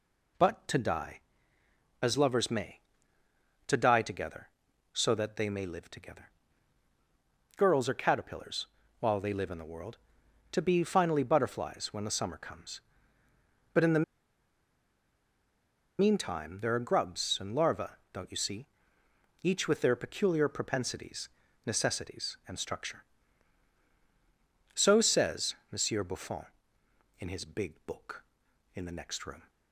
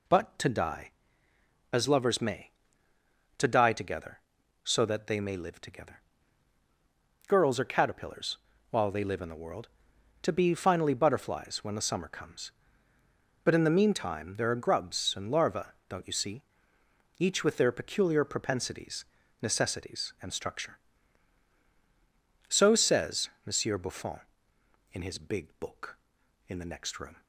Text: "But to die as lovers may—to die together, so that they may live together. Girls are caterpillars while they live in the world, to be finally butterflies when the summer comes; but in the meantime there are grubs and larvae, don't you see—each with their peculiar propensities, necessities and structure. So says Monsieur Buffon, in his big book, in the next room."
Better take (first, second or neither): second